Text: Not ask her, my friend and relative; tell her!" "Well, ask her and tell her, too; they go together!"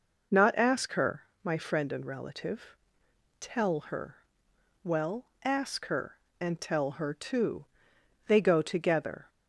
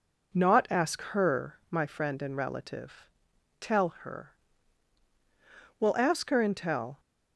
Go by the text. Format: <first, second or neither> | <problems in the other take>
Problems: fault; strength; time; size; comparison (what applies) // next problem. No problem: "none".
first | stops before "her too they go together"; at 6.9 s